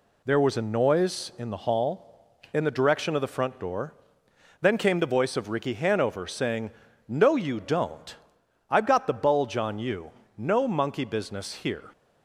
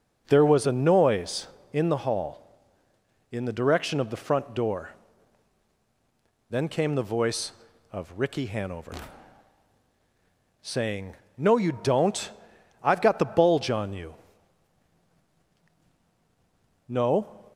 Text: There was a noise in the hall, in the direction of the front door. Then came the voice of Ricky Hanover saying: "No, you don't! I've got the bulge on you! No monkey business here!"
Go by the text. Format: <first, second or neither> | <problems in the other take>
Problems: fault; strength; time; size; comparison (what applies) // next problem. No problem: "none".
first | pauses between "Hanover" and "saying"; strong; at 8.9 s; 1.6 s long // stops before "monkey business here"; at 17.5 s